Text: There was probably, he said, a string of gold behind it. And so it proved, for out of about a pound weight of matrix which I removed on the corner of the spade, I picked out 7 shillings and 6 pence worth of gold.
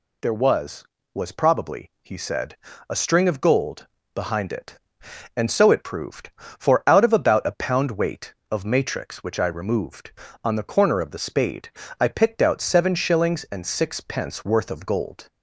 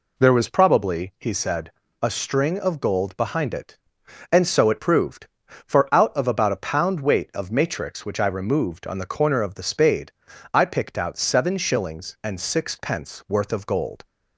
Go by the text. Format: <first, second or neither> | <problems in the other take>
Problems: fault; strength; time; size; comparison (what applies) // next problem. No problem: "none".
second | says "was" twice; at 1.1 s // pauses between "gold" and "behind"; slight; at 3.8 s; 0.28 s long